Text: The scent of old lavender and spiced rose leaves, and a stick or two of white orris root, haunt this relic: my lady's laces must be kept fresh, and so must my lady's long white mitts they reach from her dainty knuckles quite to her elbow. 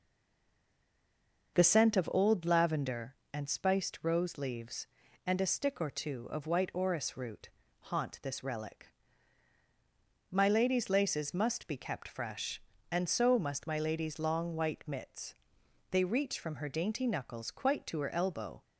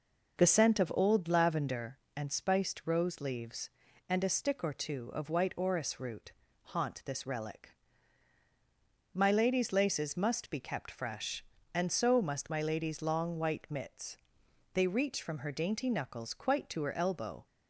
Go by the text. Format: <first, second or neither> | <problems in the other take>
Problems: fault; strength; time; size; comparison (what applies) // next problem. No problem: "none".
second | stays silent before the first word; noticeable; until 1.5 s; 1.5 s long // pauses between "mitts" and "they"; noticeable; at 15.3 s; 0.56 s long; noticeable in the second